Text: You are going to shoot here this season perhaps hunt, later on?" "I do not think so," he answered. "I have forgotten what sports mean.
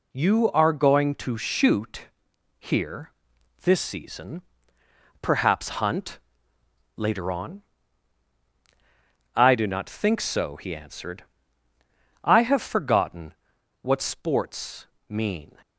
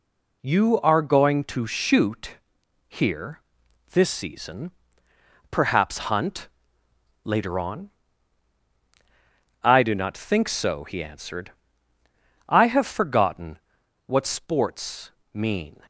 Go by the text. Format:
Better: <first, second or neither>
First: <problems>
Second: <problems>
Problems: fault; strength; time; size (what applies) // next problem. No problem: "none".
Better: neither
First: pauses between "shoot" and "here"; noticeable; at 2.0 s; 0.50 s long // pauses between "here" and "this"; noticeable; at 3.1 s; 0.52 s long // pauses between "season" and "perhaps"; noticeable; at 4.4 s; 0.80 s long // pauses between "forgotten" and "what"; noticeable; at 13.3 s; 0.48 s long // pauses between "sports" and "mean"; slight; at 14.8 s; 0.22 s long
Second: pauses between "shoot" and "here"; noticeable; at 2.3 s; 0.50 s long // pauses between "here" and "this"; noticeable; at 3.3 s; 0.52 s long // pauses between "season" and "perhaps"; noticeable; at 4.6 s; 0.80 s long // pauses between "forgotten" and "what"; noticeable; at 13.5 s; 0.48 s long // pauses between "sports" and "mean"; slight; at 15.1 s; 0.22 s long